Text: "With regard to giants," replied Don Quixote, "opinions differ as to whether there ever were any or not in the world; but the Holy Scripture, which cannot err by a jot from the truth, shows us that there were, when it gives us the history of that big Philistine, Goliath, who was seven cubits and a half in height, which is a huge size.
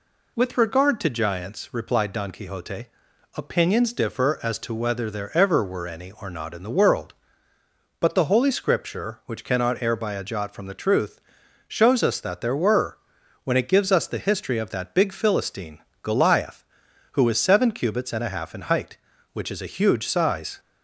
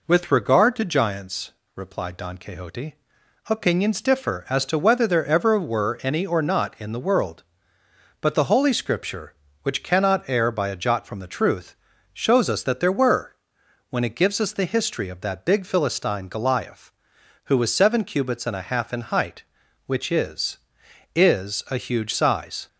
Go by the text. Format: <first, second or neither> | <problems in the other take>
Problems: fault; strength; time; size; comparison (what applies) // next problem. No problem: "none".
first | says "is" twice; at 21.1 s